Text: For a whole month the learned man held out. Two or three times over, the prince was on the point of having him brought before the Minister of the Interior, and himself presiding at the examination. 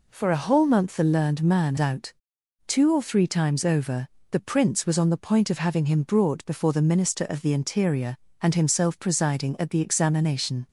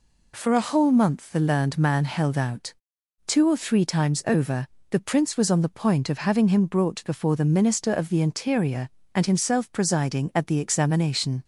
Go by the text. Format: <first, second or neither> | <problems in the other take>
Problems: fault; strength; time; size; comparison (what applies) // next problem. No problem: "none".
second | skips "held"; at 1.7 s